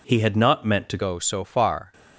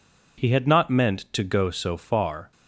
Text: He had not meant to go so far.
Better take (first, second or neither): second